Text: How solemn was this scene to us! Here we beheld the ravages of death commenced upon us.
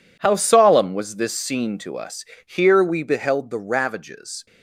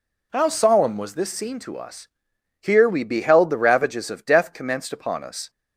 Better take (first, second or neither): second